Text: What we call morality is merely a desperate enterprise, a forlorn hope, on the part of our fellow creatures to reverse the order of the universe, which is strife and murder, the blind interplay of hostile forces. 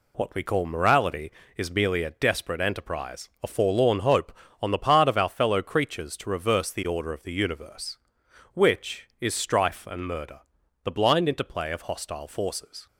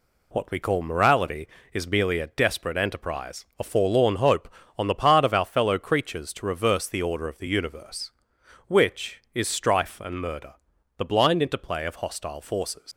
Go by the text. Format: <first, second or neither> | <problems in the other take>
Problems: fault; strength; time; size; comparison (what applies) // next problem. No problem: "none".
first | leaves "forces" unfinished; at 12.9 s; 90 ms